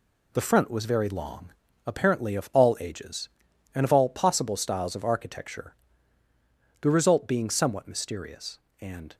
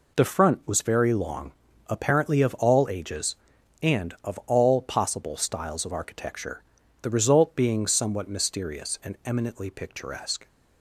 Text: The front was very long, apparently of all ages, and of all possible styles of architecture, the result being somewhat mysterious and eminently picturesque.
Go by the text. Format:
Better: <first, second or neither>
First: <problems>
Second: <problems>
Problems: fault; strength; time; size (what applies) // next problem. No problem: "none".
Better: second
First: stops before "eminently picturesque"; at 9.1 s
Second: none